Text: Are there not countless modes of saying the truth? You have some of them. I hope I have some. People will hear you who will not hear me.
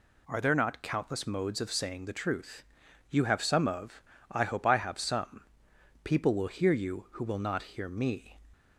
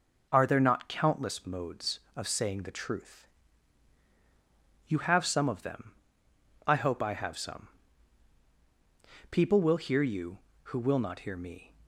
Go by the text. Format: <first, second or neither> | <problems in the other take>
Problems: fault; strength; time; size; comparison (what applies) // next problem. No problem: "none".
second | skips "them"; at 4.1 s